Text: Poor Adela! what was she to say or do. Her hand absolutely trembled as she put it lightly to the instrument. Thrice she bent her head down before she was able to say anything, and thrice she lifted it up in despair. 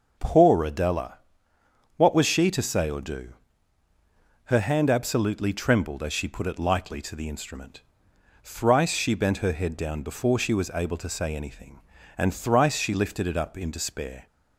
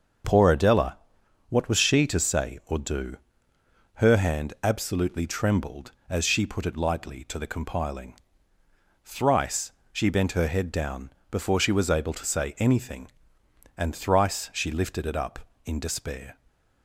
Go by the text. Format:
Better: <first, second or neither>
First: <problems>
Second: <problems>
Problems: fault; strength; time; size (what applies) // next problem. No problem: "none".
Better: first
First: none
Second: starts louder than the rest; until 1.7 s; 6.5 dB // says "compiling" for "instrument"; at 7.4 s // pauses between "Thrice" and "she"; slight; at 9.7 s; 0.20 s long // pauses between "down" and "before"; slight; at 11.0 s; 0.20 s long